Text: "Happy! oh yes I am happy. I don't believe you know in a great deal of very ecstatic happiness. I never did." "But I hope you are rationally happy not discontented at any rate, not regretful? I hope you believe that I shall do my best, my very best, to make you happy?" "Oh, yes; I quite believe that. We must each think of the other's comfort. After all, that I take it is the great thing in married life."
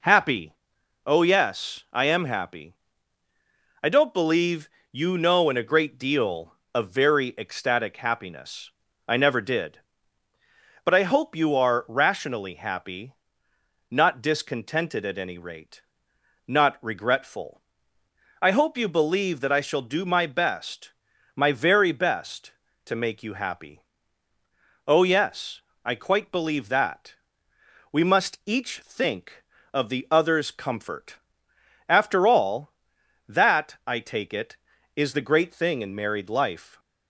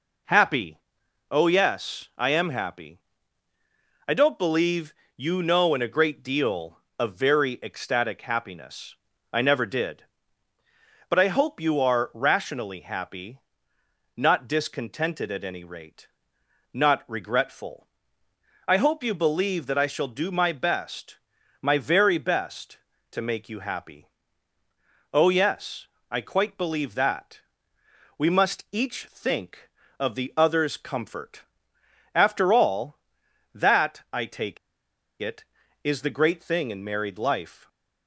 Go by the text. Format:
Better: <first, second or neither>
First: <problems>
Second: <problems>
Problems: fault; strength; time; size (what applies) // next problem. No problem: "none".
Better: first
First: pauses between "believe" and "you"; slight; at 4.6 s; 0.24 s long // pauses between "happy" and "not"; noticeable; at 13.1 s; 0.78 s long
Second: pauses between "believe" and "you"; slight; at 4.9 s; 0.24 s long // pauses between "happy" and "not"; noticeable; at 13.3 s; 0.78 s long // pauses between "take" and "it"; noticeable; at 34.5 s; 0.64 s long